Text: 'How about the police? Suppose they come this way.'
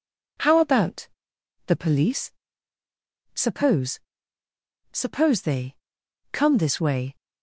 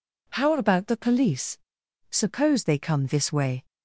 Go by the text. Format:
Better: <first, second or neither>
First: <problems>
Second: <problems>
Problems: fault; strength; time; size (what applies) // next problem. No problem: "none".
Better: second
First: pauses between "about" and "the"; noticeable; at 1.0 s; 0.60 s long // says "Suppose" twice; at 4.9 s // pauses between "they" and "come"; noticeable; at 5.7 s; 0.56 s long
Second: none